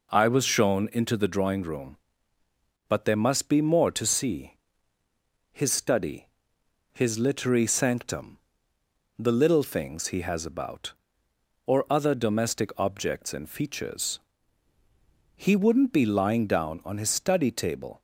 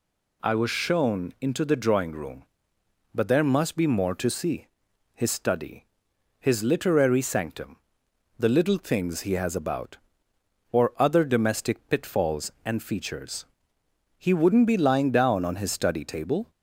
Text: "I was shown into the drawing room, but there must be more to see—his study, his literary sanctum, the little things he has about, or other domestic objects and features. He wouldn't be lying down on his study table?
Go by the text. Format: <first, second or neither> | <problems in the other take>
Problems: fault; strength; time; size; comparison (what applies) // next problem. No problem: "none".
first | says "pitfalls" for "objects"; at 11.8 s